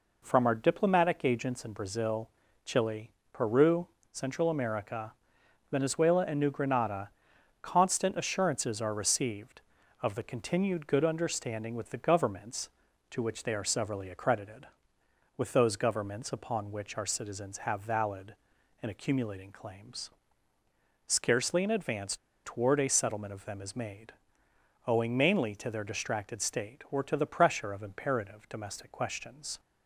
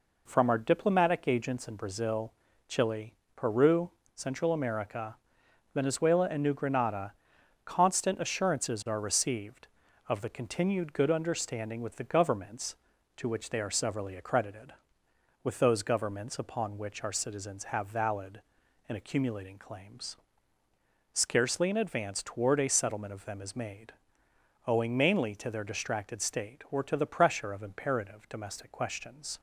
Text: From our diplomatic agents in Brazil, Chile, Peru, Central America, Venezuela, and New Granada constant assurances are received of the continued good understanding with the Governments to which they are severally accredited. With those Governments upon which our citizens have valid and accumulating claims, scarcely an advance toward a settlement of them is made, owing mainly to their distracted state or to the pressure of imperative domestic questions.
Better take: second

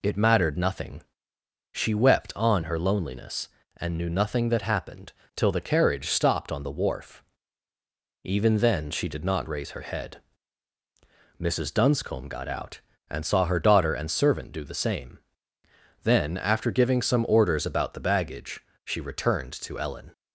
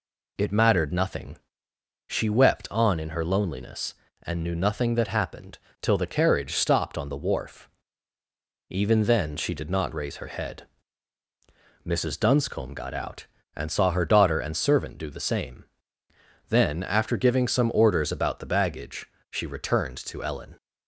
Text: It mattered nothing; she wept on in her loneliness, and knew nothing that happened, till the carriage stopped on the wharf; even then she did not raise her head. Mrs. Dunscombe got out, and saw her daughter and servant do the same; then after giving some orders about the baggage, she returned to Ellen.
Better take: second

